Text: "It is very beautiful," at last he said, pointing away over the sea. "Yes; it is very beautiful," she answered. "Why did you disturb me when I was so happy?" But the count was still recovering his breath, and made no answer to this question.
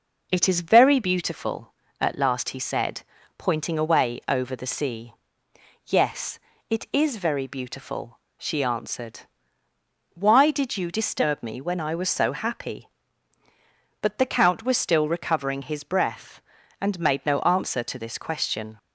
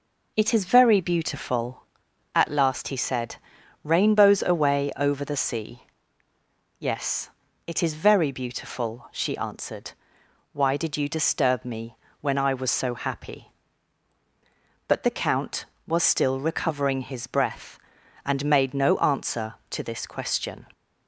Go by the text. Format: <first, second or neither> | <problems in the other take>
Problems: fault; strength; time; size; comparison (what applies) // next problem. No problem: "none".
first | says "rainbows" for "pointing"; at 3.8 s // pauses between "me" and "when"; slight; at 11.9 s; 0.24 s long